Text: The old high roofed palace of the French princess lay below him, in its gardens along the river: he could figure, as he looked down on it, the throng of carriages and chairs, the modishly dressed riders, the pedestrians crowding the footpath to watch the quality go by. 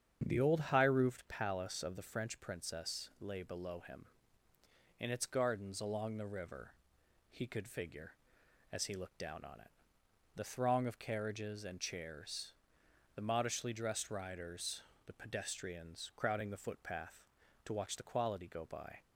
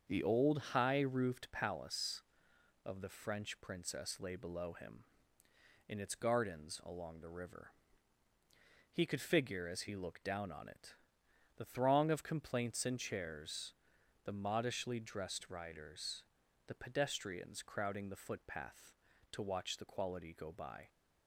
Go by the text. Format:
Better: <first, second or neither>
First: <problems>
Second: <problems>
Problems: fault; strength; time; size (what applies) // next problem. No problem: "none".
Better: first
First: starts louder than the rest; strong; until 1.2 s; 8 dB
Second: starts louder than the rest; until 1.2 s; 7 dB // says "complaints" for "carriages"; at 12.2 s